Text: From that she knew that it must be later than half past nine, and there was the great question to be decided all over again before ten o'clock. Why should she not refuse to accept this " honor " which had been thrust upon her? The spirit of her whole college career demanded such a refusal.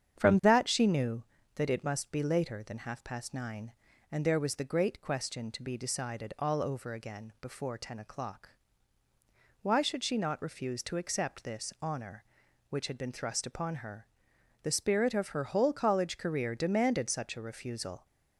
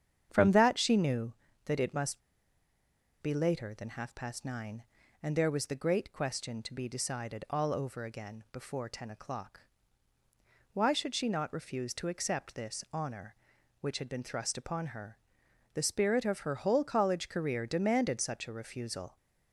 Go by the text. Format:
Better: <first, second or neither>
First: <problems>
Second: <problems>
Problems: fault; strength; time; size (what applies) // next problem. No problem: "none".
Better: first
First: starts louder than the rest; strong; until 1.2 s; 8.5 dB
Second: starts louder than the rest; strong; until 1.3 s; 8.5 dB // pauses between "must" and "be"; at 2.2 s; 1.0 s long